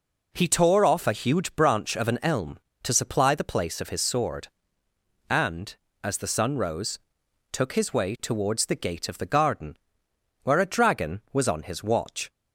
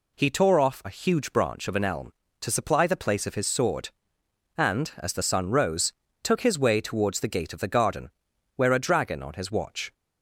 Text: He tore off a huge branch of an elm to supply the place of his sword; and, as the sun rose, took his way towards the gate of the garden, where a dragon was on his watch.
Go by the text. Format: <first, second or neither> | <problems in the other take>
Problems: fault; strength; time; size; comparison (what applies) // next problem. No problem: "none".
first | skips "was"; at 9.2 s